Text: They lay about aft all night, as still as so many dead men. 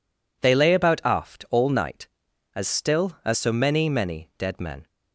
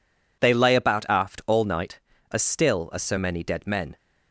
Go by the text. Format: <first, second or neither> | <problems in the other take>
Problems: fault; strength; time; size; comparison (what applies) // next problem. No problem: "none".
second | says "many" twice; at 3.8 s